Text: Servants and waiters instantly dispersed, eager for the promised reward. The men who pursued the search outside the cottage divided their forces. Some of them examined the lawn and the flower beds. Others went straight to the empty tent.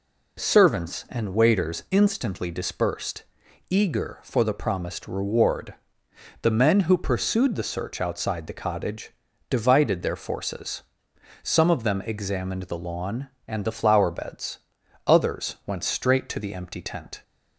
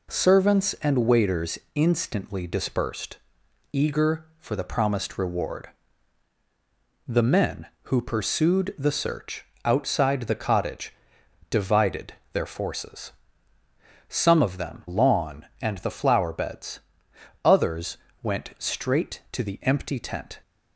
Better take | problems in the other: first | pauses between "waiters" and "instantly"; slight; at 1.5 s; 0.16 s long // pauses between "search" and "outside"; slight; at 9.4 s; 0.18 s long // pauses between "cottage" and "divided"; noticeable; at 10.9 s; 0.58 s long; also in the first // pauses between "divided" and "their"; slight; at 12.1 s; 0.20 s long // skips "examined the"; at 14.8 s // pauses between "Others" and "went"; slight; at 17.9 s; 0.26 s long

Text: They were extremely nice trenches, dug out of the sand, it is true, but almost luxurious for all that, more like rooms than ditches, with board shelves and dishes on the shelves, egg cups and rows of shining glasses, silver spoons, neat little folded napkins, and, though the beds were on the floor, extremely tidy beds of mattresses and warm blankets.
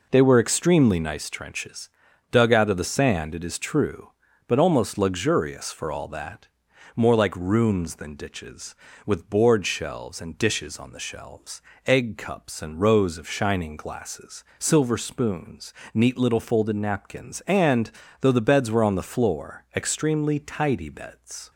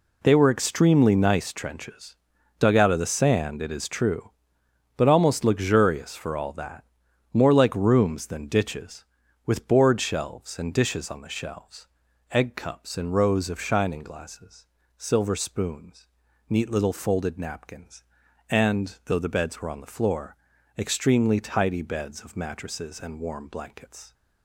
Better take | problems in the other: second | stops before "of mattresses and warm blankets"; at 21.5 s

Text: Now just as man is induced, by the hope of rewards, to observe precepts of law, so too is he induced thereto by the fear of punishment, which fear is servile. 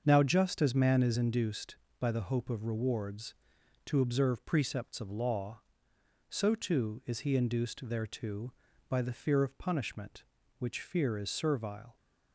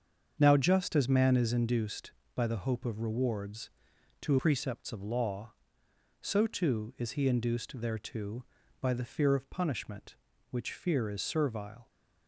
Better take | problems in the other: first | starts louder than the rest; strong; until 1.4 s; 7 dB; also in the first // skips "observe"; at 4.3 s

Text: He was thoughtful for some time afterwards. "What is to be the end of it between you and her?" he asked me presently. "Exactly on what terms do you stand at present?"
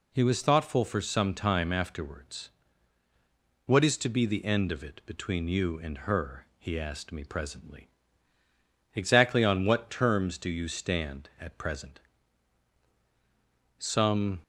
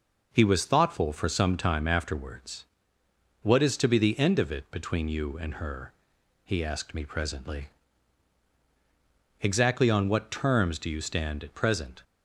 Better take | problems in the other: second | goes on to say "Some"; noticeable; from 13.7 s on; 0.64 s long

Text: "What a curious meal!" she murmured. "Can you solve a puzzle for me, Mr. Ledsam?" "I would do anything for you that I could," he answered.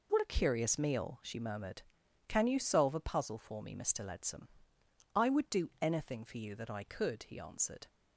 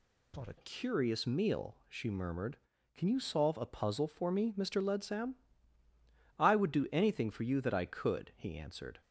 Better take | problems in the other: first | changes voice at "curious"; from 0.5 s on; 8.5 s long

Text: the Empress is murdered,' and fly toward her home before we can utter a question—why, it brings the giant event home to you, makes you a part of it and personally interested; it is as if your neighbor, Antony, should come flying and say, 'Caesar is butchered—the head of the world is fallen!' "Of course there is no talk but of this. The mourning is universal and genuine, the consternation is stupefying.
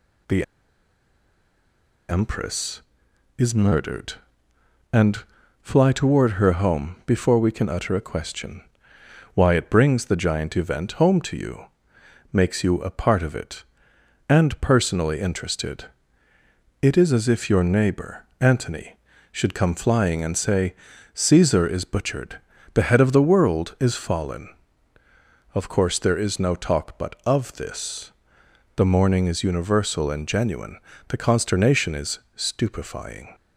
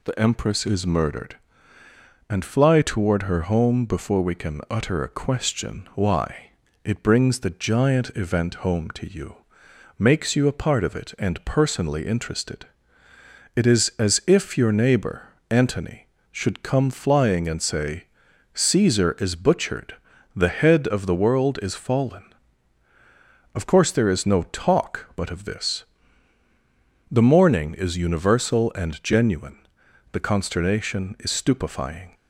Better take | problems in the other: second | pauses between "the" and "Empress"; strong; at 0.4 s; 1.6 s long // pauses between "and" and "fly"; at 5.2 s; 0.38 s long // pauses between "is" and "stupefying"; slight; at 32.1 s; 0.16 s long

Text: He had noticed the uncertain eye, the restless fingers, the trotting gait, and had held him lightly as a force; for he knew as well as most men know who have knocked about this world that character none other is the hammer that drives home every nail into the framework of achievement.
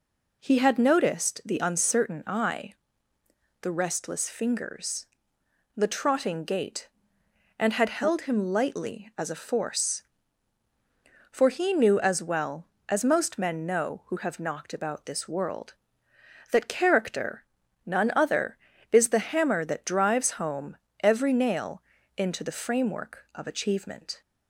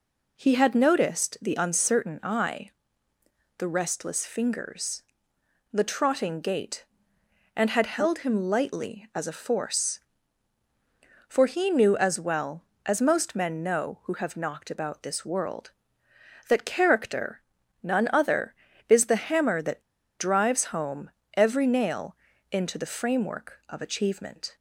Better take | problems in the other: first | pauses between "character" and "none"; at 17.4 s; 0.42 s long; also in the first // pauses between "that" and "drives"; at 19.8 s; 0.38 s long // pauses between "home" and "every"; slight; at 21.1 s; 0.24 s long; slight in the first // pauses between "nail" and "into"; slight; at 22.1 s; 0.36 s long; slight in the first

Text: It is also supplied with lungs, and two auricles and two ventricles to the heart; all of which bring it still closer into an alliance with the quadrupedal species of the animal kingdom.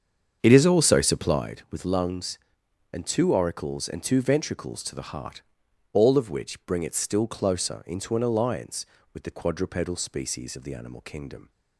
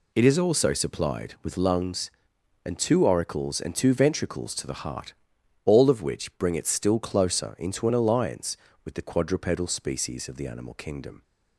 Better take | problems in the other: second | starts louder than the rest; strong; until 1.5 s; 7 dB

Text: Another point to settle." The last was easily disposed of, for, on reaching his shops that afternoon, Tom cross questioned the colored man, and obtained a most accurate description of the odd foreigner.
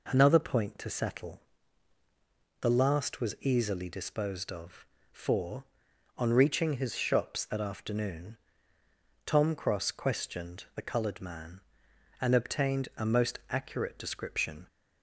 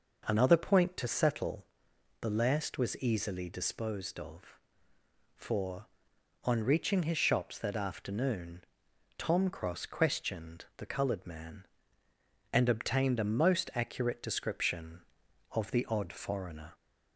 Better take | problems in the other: second | stops before "of the odd foreigner"; at 14.6 s

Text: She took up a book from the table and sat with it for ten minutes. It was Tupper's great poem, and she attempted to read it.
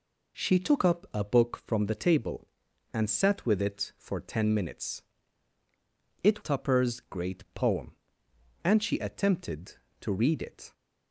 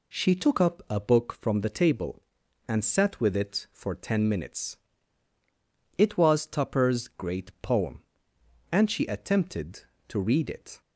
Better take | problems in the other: second | skips "was"; at 6.4 s

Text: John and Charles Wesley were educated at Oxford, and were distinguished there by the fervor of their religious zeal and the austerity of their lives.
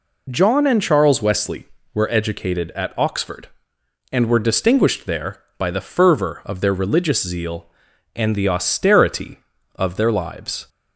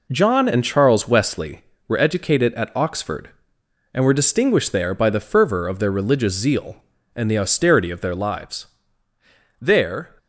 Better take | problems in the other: first | goes on to say "There"; from 9.5 s on; 0.58 s long

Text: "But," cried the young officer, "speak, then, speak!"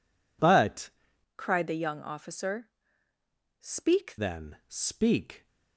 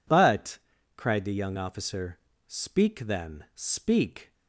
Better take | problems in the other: second | changes voice from "cried" to "speak"; from 1.3 to 4.1 s; 2.8 s long

